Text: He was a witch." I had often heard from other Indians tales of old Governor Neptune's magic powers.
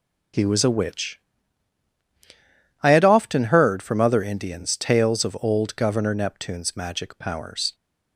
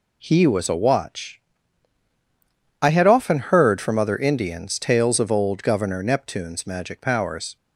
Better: first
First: none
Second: says "watch" for "witch"; at 0.7 s

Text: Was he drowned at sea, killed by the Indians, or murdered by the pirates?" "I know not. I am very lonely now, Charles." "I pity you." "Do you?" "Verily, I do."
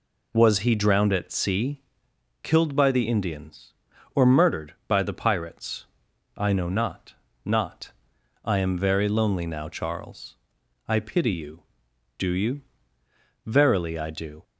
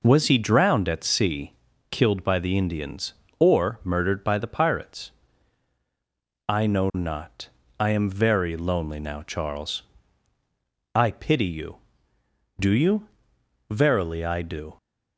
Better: second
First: says "not" twice; at 7.4 s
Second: none

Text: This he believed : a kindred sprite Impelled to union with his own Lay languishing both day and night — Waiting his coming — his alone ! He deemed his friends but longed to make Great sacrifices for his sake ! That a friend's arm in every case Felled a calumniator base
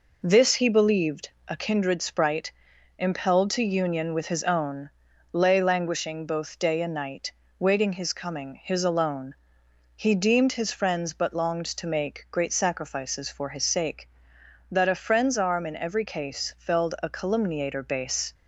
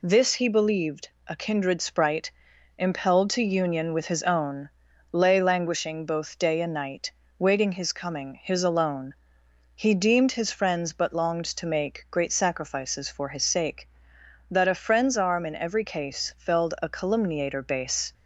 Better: second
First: starts louder than the rest; noticeable; until 1.9 s; 4.5 dB // pauses between "sprite" and "Impelled"; noticeable; at 2.4 s; 0.48 s long // pauses between "own" and "Lay"; at 4.8 s; 0.42 s long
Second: pauses between "sprite" and "Impelled"; noticeable; at 2.2 s; 0.48 s long // pauses between "own" and "Lay"; at 4.6 s; 0.42 s long

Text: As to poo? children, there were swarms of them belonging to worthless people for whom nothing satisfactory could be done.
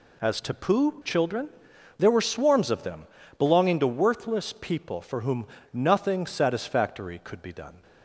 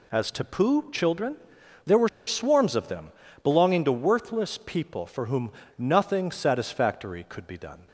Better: first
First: pauses between "them" and "belonging"; slight; at 3.0 s; 0.34 s long // pauses between "whom" and "nothing"; slight; at 5.4 s; 0.28 s long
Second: pauses between "were" and "swarms"; slight; at 2.0 s; 0.17 s long // pauses between "them" and "belonging"; slight; at 3.0 s; 0.34 s long // pauses between "whom" and "nothing"; slight; at 5.5 s; 0.28 s long

